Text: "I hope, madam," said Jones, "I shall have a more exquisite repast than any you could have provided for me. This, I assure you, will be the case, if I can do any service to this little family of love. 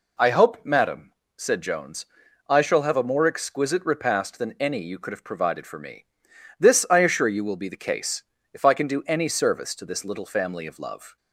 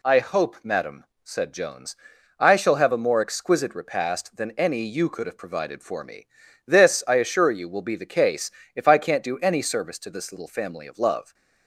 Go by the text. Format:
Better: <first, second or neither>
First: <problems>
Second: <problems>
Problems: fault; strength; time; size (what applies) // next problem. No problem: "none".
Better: first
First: none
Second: says "can't" for "can"; at 8.9 s